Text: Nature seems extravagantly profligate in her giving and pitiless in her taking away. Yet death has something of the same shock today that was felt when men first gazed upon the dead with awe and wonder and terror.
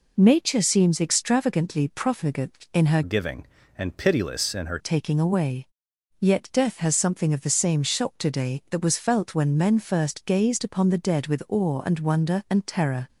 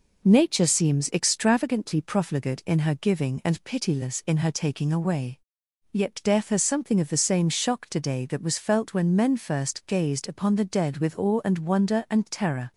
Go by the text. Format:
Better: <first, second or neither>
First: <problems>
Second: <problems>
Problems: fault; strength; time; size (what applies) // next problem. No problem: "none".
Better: second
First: changes voice from "giving" to "her"; from 3.0 to 4.7 s; 1.7 s long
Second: none